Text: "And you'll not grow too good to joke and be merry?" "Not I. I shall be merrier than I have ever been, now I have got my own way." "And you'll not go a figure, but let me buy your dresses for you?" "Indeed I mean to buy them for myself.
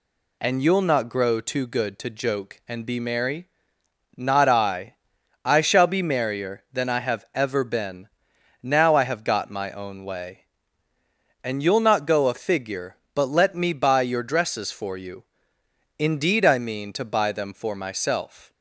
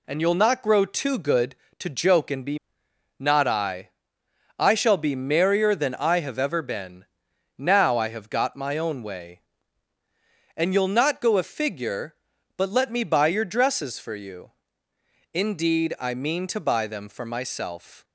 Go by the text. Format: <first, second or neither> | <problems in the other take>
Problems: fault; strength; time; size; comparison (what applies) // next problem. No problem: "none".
first | skips "merry"; at 2.8 s